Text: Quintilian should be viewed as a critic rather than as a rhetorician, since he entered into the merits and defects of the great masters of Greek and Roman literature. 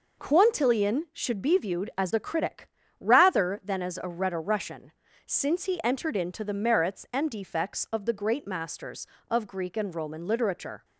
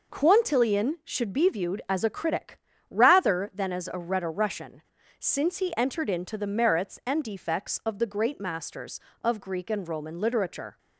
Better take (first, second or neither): neither